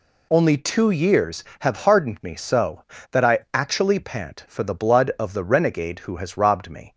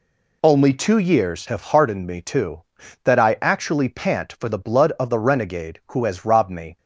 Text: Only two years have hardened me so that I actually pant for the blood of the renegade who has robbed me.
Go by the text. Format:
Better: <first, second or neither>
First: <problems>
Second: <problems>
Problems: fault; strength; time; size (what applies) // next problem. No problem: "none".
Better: first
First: none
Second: says "too" for "so"; at 2.2 s